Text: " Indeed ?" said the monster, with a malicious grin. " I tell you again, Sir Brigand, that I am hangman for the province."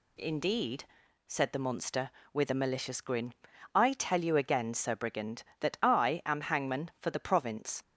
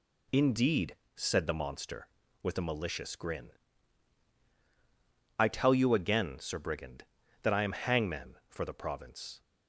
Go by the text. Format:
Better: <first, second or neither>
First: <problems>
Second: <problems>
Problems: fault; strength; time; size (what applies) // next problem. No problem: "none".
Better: second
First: changes voice at "Indeed"; from 0.1 s on; 7.7 s long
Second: none